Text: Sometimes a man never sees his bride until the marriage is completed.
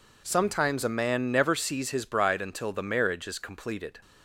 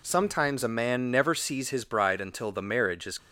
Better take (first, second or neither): first